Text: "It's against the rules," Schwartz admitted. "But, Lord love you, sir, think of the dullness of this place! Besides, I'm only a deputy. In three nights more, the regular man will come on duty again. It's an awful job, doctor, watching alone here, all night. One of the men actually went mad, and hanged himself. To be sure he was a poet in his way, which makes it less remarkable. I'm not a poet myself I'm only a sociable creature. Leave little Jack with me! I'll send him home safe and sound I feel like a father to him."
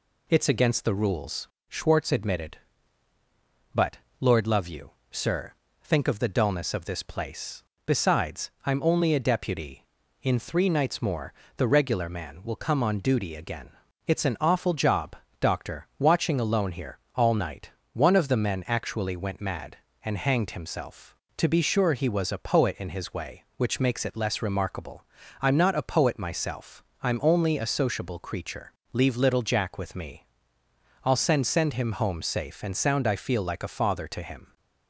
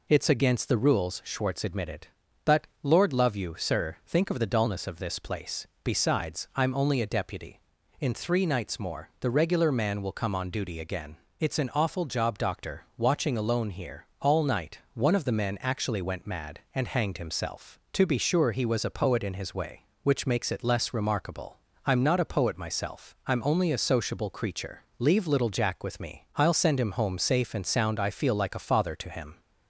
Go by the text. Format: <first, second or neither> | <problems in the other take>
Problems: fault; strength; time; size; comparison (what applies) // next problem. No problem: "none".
second | pauses between "myself" and "I'm"; slight; at 26.8 s; 0.20 s long // says "send" twice; at 31.4 s